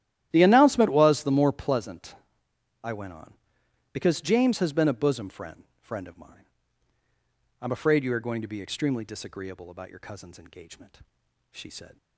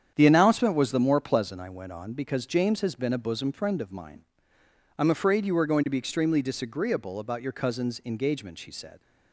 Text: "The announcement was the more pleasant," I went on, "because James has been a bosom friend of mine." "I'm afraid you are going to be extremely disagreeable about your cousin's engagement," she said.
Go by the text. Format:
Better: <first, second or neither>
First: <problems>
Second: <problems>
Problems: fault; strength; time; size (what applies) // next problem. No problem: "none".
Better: second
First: starts louder than the rest; strong; until 1.3 s; 12.5 dB // says "friend" twice; at 5.8 s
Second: starts louder than the rest; strong; until 1.1 s; 8.5 dB